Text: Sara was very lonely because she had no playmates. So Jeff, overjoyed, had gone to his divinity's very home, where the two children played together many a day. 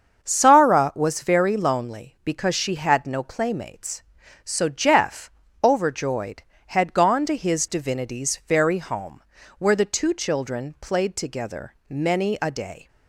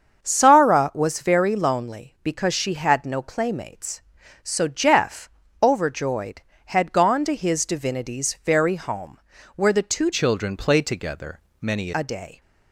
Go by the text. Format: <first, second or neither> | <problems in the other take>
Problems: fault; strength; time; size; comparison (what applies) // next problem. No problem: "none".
first | starts louder than the rest; until 1.2 s; 7 dB; also in the first // changes voice from "children" to "many"; from 10.1 to 11.9 s; 1.8 s long // pauses between "together" and "many"; slight; at 11.3 s; 0.22 s long; slight in the first